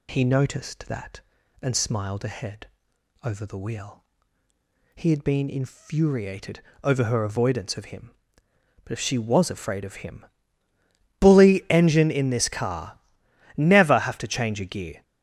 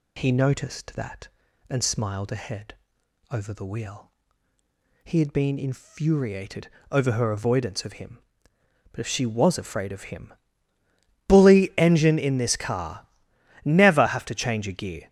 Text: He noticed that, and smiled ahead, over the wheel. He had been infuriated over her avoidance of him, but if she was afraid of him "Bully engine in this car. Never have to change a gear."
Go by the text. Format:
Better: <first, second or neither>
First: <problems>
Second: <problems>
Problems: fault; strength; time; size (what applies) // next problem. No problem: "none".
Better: neither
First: pauses between "infuriated" and "over"; slight; at 6.6 s; 0.22 s long // pauses between "him" and "Bully"; noticeable; at 10.2 s; 0.96 s long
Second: pauses between "infuriated" and "over"; slight; at 6.6 s; 0.22 s long // pauses between "him" and "Bully"; noticeable; at 10.3 s; 0.96 s long